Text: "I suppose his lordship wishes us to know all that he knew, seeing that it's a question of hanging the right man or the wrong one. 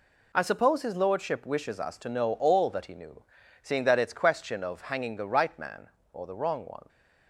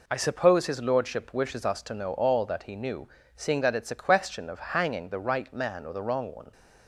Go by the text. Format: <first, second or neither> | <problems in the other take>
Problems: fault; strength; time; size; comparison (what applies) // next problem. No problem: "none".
second | skips "a"; at 4.1 s